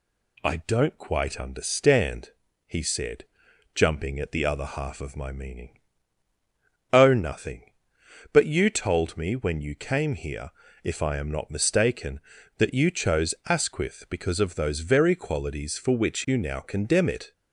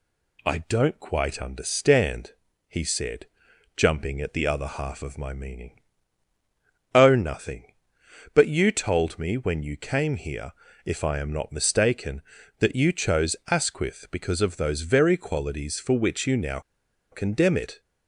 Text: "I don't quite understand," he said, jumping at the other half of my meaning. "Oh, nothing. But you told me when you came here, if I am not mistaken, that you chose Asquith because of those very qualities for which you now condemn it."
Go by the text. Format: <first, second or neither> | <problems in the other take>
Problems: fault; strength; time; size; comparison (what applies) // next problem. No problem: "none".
first | pauses between "now" and "condemn"; noticeable; at 16.5 s; 0.51 s long